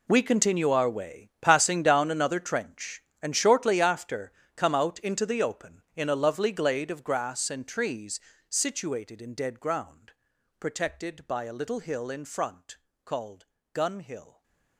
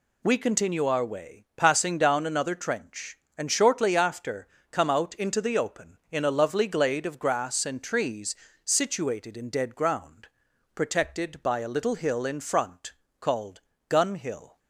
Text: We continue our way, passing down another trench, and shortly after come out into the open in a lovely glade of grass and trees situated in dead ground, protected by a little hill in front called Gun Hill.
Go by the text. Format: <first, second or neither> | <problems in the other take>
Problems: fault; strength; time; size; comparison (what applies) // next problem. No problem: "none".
second | gets quieter; strong; throughout; 17 dB // pauses between "after" and "come"; slight; at 4.3 s; 0.24 s long; slight in the second // pauses between "trees" and "situated"; slight; at 8.2 s; 0.28 s long; slight in the second // pauses between "front" and "called"; slight; at 12.7 s; 0.26 s long; slight in the second // pauses between "called" and "Gun"; slight; at 13.4 s; 0.26 s long; slight in the second // stays silent after the last word; slight; from 14.2 s on; 0.5 s long